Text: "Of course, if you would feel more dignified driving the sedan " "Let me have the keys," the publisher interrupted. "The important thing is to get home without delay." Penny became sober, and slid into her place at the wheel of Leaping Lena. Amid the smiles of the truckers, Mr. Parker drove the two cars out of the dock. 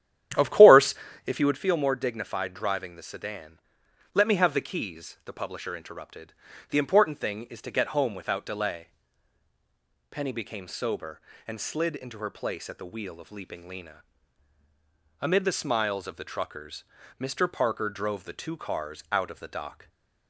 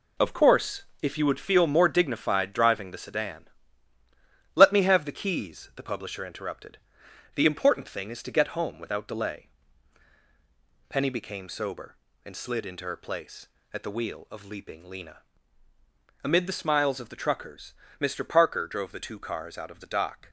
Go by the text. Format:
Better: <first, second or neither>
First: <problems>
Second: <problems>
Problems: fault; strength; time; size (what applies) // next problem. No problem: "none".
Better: second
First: starts louder than the rest; strong; until 1.7 s; 10.5 dB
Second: none